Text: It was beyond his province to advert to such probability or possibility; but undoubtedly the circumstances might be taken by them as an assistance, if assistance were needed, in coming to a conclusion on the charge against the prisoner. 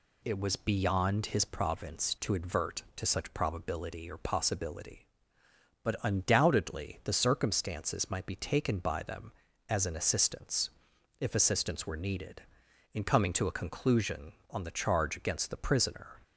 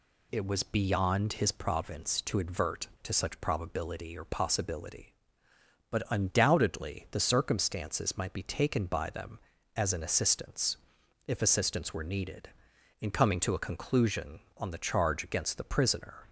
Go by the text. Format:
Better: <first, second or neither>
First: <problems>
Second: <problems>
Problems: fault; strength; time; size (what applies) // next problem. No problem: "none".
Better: neither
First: none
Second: none